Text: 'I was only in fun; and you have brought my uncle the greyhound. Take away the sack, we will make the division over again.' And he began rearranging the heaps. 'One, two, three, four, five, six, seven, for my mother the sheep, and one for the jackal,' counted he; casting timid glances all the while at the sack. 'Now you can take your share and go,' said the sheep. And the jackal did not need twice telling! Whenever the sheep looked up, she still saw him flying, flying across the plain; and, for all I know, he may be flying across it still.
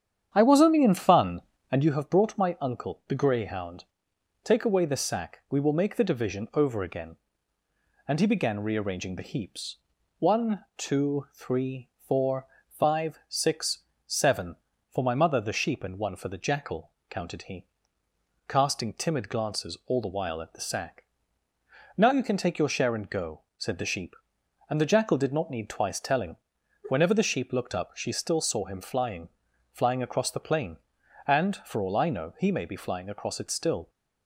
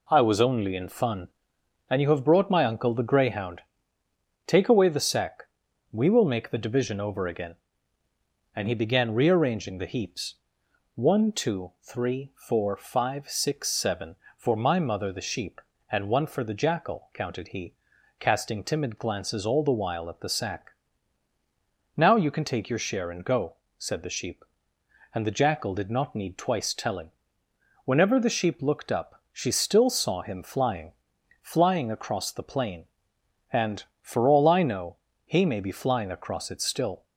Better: second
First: starts louder than the rest; strong; until 2.1 s; 8.5 dB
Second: none

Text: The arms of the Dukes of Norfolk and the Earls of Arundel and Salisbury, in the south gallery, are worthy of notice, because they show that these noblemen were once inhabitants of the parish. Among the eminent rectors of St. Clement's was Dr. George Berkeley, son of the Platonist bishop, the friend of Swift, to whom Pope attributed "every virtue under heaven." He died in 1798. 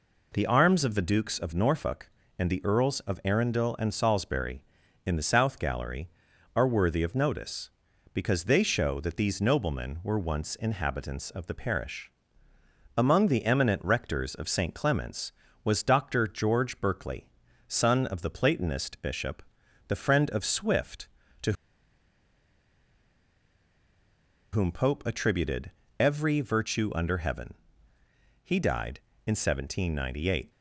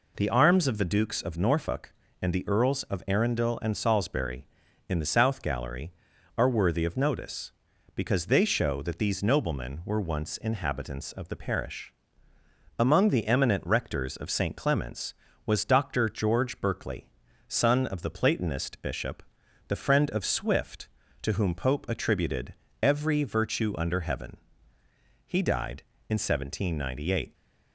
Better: second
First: pauses between "to" and "whom"; strong; at 21.5 s; 3.0 s long // pauses between "attributed" and "every"; slight; at 25.7 s; 0.30 s long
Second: pauses between "attributed" and "every"; slight; at 22.5 s; 0.30 s long

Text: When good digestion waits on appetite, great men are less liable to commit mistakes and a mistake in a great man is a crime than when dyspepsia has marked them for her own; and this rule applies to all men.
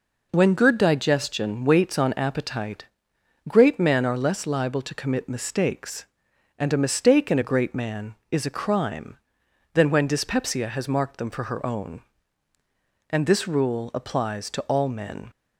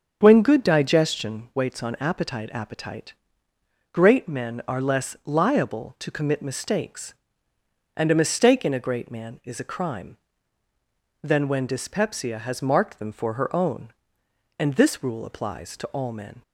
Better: first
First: none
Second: starts louder than the rest; strong; until 1.2 s; 7 dB // says "appetite" twice; at 2.5 s

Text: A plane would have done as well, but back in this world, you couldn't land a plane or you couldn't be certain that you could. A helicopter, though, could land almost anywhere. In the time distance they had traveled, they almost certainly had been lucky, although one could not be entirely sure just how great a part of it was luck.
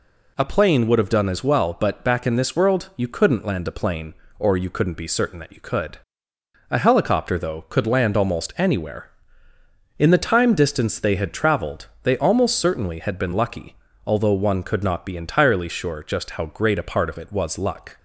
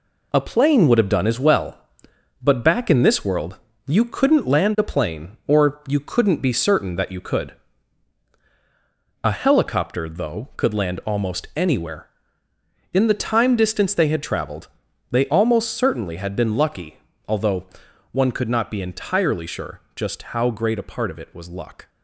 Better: first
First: none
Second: gets quieter; throughout; 6.5 dB // pauses between "although" and "one"; noticeable; at 17.6 s; 0.46 s long

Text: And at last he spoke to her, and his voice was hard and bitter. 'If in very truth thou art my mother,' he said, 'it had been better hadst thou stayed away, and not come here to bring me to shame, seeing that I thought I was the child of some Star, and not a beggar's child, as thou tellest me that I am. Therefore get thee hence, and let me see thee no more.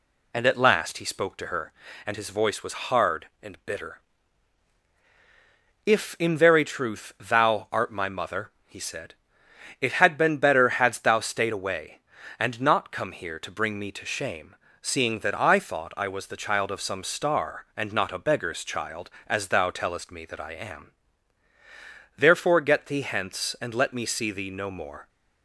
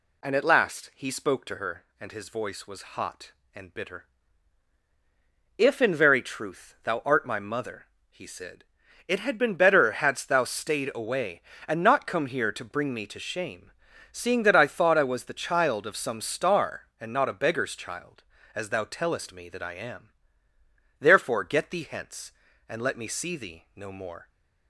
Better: first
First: none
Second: says "hot" for "hard"; at 2.9 s

